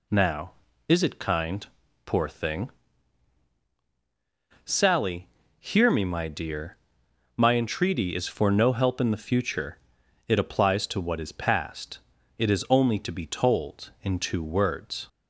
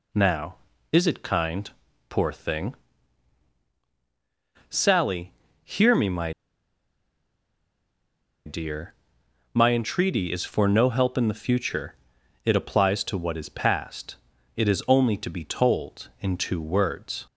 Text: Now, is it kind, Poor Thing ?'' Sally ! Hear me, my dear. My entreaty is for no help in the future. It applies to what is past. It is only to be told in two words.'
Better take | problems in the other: first | pauses between "my" and "dear"; strong; at 6.3 s; 2.1 s long

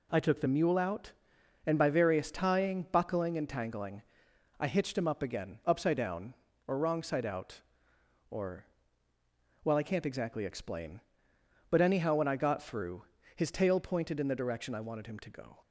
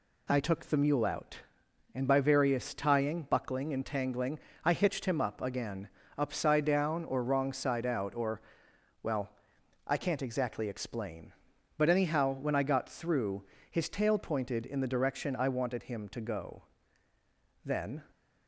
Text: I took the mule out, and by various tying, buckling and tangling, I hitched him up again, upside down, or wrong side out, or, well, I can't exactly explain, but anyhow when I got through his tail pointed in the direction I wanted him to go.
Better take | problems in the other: first | pauses between "through" and "his"; slight; at 13.4 s; 0.28 s long; slight in the first // goes on to say "Then"; slight; from 17.6 s on; 0.38 s long

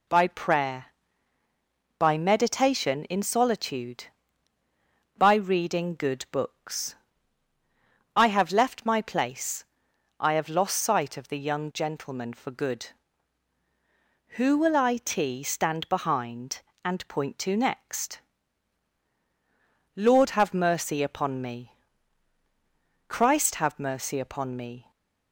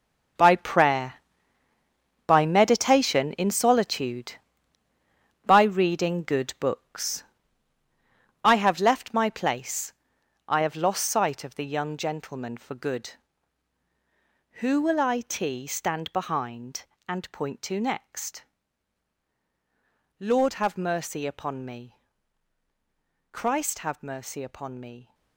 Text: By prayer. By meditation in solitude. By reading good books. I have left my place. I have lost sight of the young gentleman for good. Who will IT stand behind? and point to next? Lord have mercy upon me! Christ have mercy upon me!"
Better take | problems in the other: first | gets quieter; strong; throughout; 14 dB

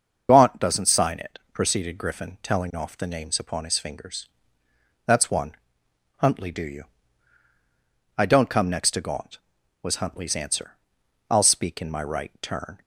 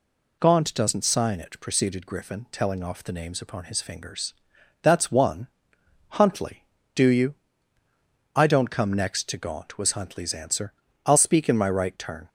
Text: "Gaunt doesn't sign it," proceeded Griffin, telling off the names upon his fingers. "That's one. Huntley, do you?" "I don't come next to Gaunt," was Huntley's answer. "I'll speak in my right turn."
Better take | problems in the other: second | loses the start of "Gaunt"; at 0.2 s; 45 ms // starts louder than the rest; until 1.3 s; 6.5 dB

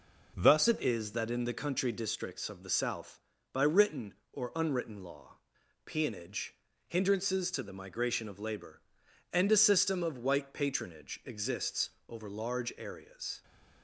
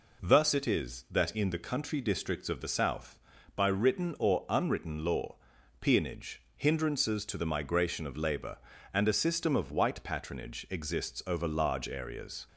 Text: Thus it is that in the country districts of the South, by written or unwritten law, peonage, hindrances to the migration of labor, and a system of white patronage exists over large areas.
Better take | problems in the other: second | changes voice at "it"; from 0.6 s on; 12.8 s long // pauses between "exists" and "over"; slight; at 11.9 s; 0.18 s long

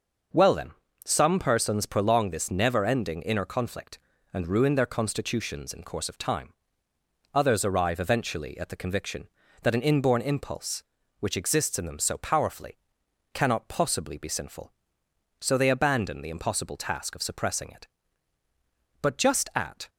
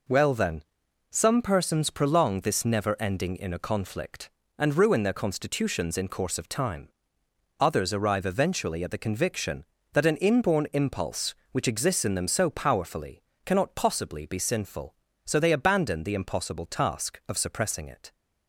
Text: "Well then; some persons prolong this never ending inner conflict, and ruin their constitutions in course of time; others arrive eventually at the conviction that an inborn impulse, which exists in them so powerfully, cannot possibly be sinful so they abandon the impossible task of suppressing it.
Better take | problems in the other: second | goes on to say "But just at"; noticeable; from 19.0 s on; 0.88 s long

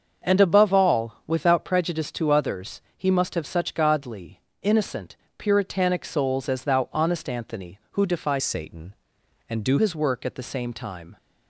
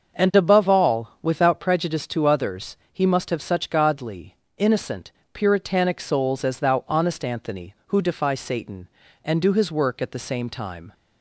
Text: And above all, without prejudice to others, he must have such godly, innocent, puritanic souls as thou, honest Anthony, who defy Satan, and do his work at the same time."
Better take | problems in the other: second | starts louder than the rest; until 1.3 s; 6.5 dB; also in the second // changes voice from "Satan" to "do"; from 8.3 to 9.7 s; 1.4 s long

